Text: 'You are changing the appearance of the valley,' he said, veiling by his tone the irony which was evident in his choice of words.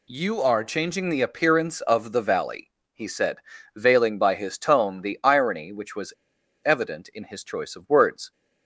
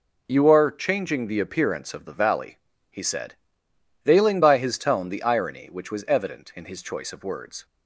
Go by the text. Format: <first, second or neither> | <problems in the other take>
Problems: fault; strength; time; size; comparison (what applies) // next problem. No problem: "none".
second | pauses between "was" and "evident"; noticeable; at 6.1 s; 0.50 s long